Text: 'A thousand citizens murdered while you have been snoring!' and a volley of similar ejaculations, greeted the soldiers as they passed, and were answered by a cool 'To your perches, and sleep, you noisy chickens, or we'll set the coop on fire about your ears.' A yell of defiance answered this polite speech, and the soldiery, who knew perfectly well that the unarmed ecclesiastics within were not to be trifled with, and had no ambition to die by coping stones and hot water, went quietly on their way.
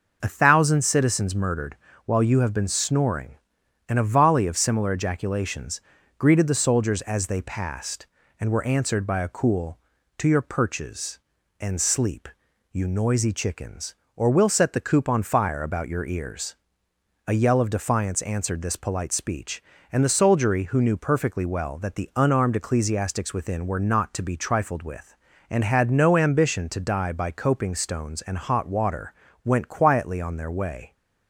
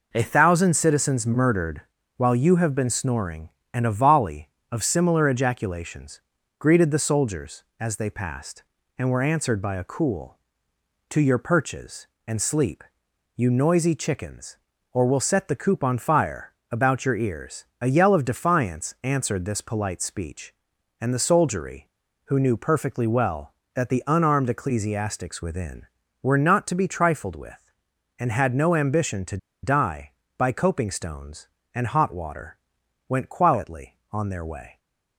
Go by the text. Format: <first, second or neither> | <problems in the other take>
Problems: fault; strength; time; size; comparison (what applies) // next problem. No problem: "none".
first | pauses between "murdered" and "while"; slight; at 1.8 s; 0.34 s long; slight in the first // pauses between "fire" and "about"; slight; at 16.5 s; 0.16 s long // pauses between "to" and "die"; slight; at 29.3 s; 0.26 s long